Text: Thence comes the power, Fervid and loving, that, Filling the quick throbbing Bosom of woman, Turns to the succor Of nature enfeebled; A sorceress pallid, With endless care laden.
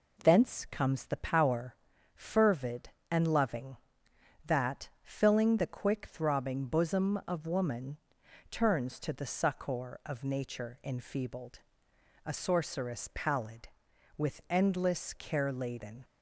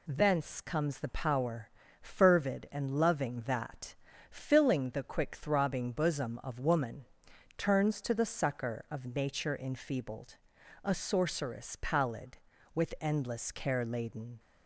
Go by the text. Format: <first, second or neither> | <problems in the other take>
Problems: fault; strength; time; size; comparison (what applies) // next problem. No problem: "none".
neither | none